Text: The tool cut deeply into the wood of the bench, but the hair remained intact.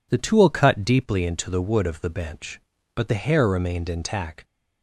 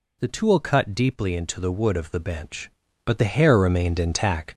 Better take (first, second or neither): first